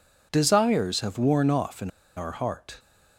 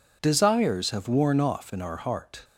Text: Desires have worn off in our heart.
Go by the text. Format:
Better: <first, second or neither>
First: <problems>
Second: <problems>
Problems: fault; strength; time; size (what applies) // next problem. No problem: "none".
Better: second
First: pauses between "in" and "our"; slight; at 1.8 s; 0.27 s long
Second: none